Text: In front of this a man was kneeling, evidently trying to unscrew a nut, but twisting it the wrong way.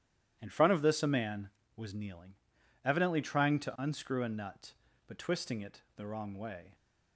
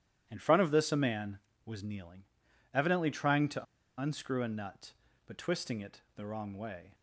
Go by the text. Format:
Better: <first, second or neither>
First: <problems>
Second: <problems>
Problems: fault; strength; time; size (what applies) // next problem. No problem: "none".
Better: first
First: pauses between "it" and "the"; slight; at 5.8 s; 0.16 s long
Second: pauses between "to" and "unscrew"; slight; at 3.6 s; 0.35 s long // pauses between "it" and "the"; slight; at 6.0 s; 0.16 s long